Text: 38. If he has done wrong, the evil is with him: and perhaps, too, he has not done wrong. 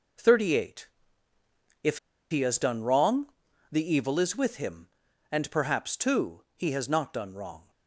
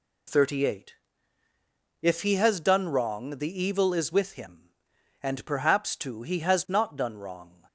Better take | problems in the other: second | pauses between "If" and "he"; slight; at 1.9 s; 0.32 s long

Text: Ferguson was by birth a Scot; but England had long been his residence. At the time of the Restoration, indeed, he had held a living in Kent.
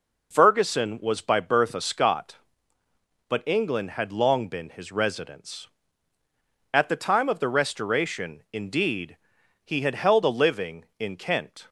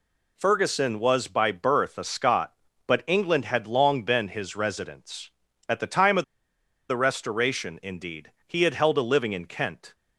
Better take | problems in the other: first | pauses between "of" and "the"; noticeable; at 6.2 s; 0.65 s long

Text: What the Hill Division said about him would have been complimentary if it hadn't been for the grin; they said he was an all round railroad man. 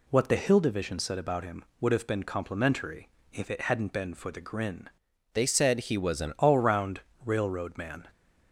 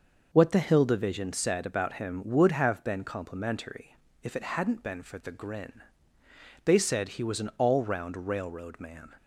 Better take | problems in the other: second | pauses between "complimentary" and "if"; slight; at 3.0 s; 0.24 s long; slight in the second // changes voice from "they" to "an"; from 5.3 to 6.3 s; 1.0 s long // pauses between "round" and "railroad"; slight; at 7.0 s; 0.24 s long

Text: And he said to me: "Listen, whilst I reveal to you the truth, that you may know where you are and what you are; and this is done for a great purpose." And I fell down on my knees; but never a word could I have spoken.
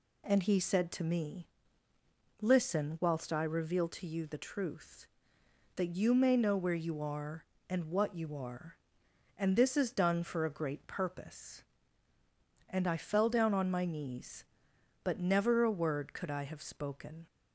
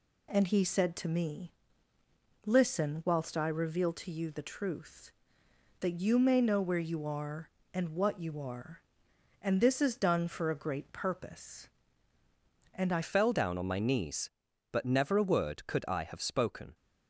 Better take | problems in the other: first | changes voice at "fell"; from 13.0 s on; 3.7 s long

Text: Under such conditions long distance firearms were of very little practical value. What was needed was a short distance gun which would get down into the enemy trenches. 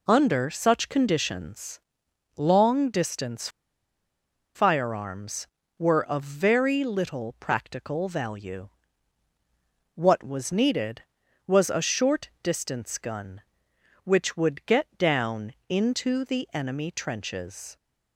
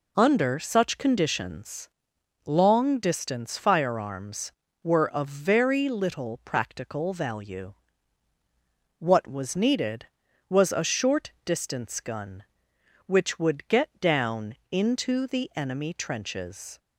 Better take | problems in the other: second | pauses between "conditions" and "long"; noticeable; at 1.7 s; 0.56 s long; noticeable in the second // pauses between "distance" and "firearms"; at 3.4 s; 1.0 s long // pauses between "down" and "into"; slight; at 15.5 s; 0.16 s long; slight in the second

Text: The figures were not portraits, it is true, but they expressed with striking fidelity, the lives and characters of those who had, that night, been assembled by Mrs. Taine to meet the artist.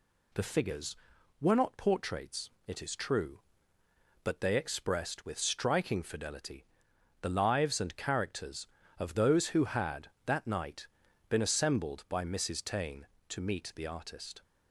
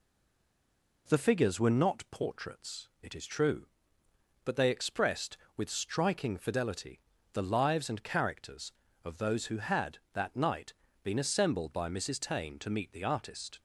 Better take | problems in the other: first | stays silent before the first word; until 1.0 s; 1.0 s long

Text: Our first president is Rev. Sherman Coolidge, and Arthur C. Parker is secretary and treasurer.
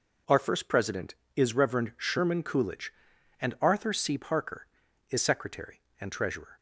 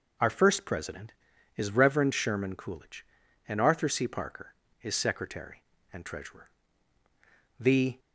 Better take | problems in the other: first | goes on to say "The"; slight; from 7.5 s on; 0.40 s long

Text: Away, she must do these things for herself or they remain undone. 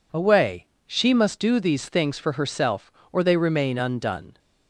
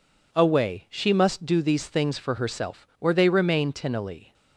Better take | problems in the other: first | says "tinily" for "undone"; at 3.7 s

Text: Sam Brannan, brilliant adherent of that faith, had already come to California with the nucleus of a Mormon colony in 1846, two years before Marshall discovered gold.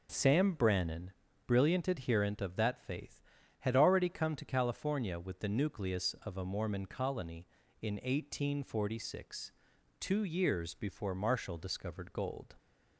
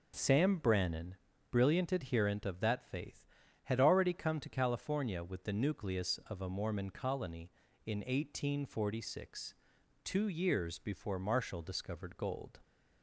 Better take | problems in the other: neither | none

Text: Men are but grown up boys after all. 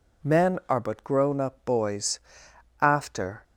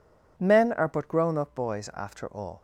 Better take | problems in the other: second | pauses between "boys" and "after"; noticeable; at 2.1 s; 0.62 s long // stops before "all"; at 3.4 s

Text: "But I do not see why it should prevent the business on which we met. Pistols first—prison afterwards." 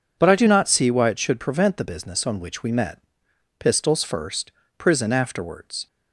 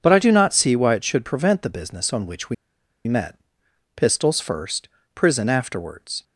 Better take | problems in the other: first | pauses between "we" and "met"; noticeable; at 2.5 s; 0.52 s long

